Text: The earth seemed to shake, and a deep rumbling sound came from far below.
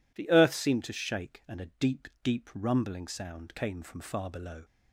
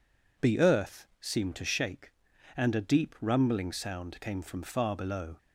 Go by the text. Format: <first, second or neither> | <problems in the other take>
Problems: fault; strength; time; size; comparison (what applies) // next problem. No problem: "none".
second | says "deep" twice; at 2.2 s